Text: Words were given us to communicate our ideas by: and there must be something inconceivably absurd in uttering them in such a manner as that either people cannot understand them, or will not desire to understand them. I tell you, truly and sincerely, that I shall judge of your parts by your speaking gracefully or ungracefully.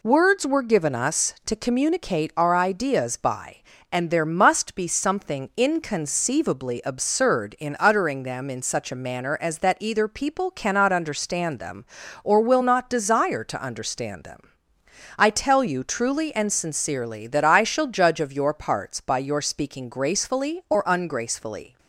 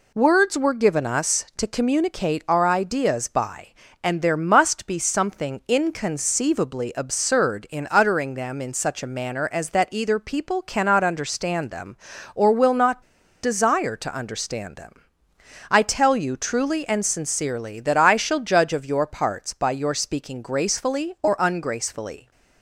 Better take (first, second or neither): first